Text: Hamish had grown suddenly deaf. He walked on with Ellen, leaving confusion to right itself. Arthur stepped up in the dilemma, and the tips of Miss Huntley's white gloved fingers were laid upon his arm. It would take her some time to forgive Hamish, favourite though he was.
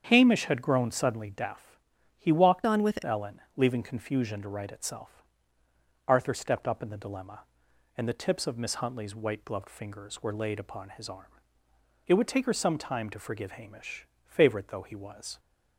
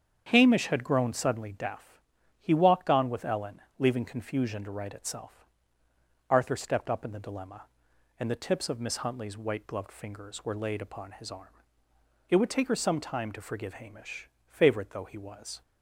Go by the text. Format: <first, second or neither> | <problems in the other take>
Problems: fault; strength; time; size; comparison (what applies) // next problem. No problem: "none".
second | starts louder than the rest; strong; until 1.1 s; 8 dB; strong in the second // changes voice from "on" to "with"; from 2.6 to 3.0 s; 0.4 s long